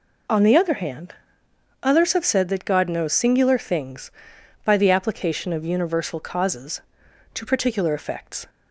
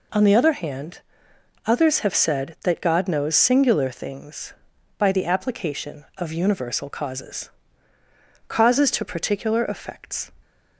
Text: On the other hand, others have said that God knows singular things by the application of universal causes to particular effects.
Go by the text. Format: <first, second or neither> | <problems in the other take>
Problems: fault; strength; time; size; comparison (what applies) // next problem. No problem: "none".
first | says "causes" twice; at 8.4 s